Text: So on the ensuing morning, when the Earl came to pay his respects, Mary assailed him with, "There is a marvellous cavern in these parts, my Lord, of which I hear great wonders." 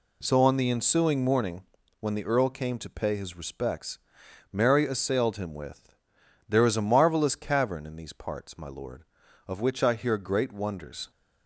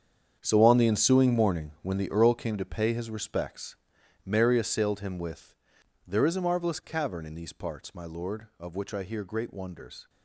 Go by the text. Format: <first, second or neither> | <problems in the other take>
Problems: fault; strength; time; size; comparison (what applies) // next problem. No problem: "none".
first | gets quieter; strong; throughout; 13 dB